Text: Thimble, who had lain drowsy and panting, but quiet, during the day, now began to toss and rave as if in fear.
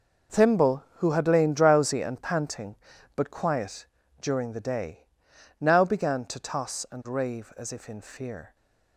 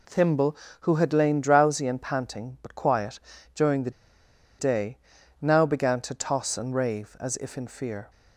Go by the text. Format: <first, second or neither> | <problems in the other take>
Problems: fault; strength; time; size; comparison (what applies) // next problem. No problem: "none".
first | pauses between "the" and "day"; noticeable; at 3.8 s; 0.68 s long